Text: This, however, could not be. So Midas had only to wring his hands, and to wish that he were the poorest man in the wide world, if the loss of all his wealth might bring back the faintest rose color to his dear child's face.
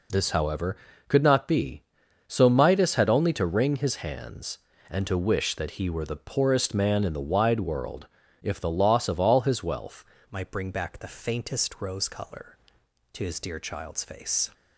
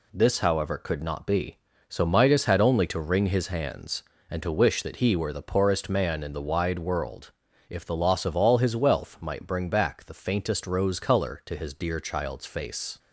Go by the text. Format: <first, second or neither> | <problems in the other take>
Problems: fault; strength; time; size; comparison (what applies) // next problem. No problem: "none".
second | changes voice at "might"; from 10.2 s on; 4.2 s long